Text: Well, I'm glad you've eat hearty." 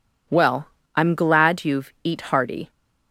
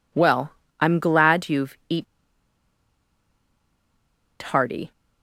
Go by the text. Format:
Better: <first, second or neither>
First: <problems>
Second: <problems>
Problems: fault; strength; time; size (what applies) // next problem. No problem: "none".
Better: first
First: none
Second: pauses between "eat" and "hearty"; strong; at 2.0 s; 2.3 s long